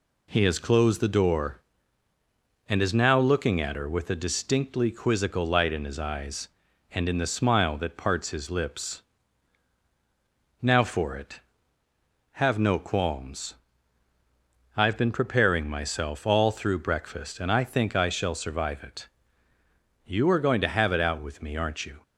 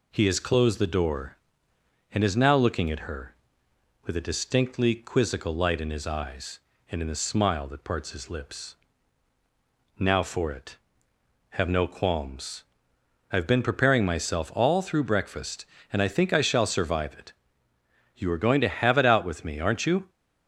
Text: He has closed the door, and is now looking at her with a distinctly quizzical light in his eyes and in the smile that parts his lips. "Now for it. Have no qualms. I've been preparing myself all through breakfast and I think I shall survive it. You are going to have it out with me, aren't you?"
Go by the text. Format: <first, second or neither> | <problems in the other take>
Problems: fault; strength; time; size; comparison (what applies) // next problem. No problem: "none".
neither | none